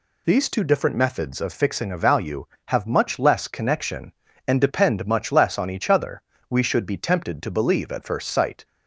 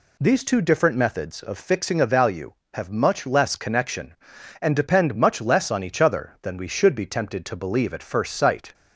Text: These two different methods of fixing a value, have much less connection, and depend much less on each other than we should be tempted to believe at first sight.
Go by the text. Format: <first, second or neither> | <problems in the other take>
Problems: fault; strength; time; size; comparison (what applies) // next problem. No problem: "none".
second | skips "than"; at 6.3 s